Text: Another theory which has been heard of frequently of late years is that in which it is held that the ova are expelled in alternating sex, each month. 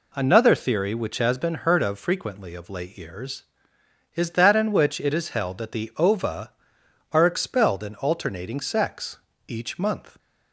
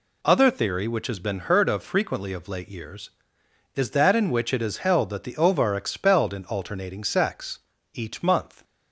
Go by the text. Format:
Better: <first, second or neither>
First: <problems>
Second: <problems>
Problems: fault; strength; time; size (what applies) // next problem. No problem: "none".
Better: first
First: none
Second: says "Other" for "Another"; at 0.2 s